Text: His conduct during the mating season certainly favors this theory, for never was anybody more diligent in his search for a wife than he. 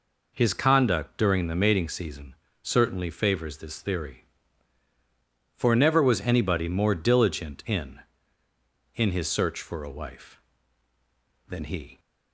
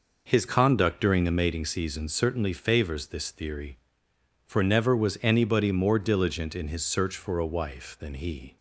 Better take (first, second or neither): second